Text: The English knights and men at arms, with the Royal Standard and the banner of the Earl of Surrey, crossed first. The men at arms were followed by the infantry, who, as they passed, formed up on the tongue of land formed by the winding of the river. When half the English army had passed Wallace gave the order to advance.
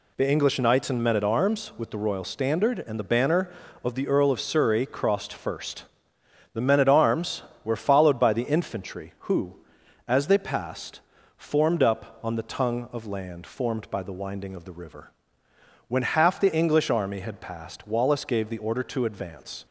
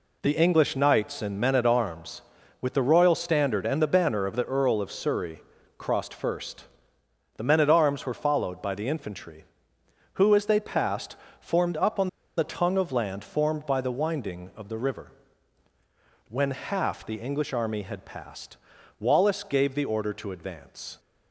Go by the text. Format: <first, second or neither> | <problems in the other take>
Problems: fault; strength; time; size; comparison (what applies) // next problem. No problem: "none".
first | pauses between "on" and "the"; slight; at 12.0 s; 0.29 s long // pauses between "passed" and "Wallace"; at 18.5 s; 0.40 s long